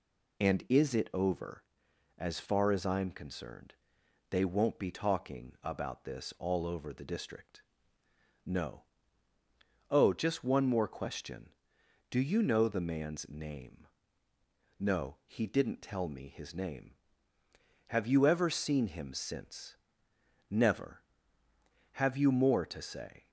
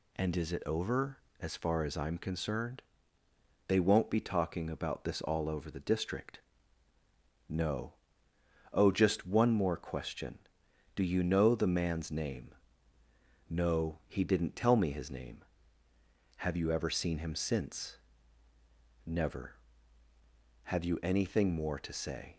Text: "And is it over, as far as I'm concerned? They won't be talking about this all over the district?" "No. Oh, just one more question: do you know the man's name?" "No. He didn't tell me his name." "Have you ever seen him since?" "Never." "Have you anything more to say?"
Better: second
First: skips "anything"; at 22.2 s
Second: none

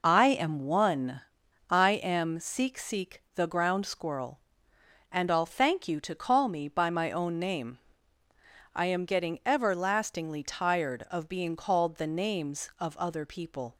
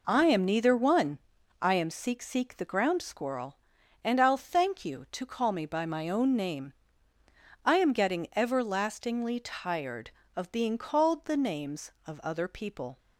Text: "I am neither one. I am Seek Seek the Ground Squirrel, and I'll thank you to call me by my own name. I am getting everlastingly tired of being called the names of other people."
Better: second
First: skips "neither"; at 0.5 s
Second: none

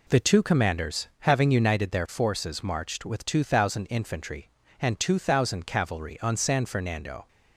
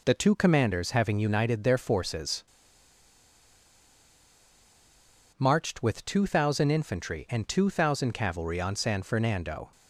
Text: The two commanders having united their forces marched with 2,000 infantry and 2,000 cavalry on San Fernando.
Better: first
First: none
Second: pauses between "forces" and "marched"; strong; at 2.4 s; 2.9 s long

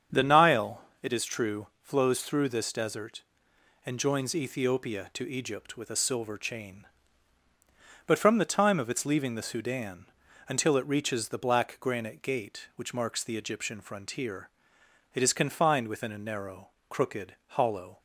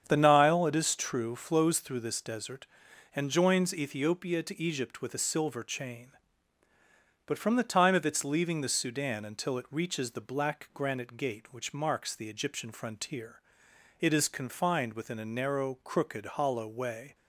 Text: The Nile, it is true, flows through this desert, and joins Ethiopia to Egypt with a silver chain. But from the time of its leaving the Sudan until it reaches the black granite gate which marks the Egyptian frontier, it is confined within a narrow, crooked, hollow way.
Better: second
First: starts louder than the rest; strong; until 1.3 s; 7.5 dB // pauses between "Sudan" and "until"; at 10.0 s; 0.42 s long // stops before "way"; at 17.9 s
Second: starts louder than the rest; strong; until 1.0 s; 8 dB

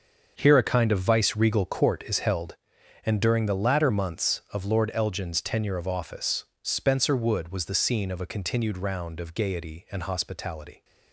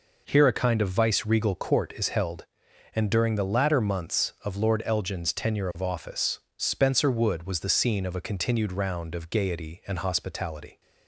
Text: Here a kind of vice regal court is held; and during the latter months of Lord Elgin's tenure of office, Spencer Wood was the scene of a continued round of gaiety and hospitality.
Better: second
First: gets quieter; strong; throughout; 11.5 dB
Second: none

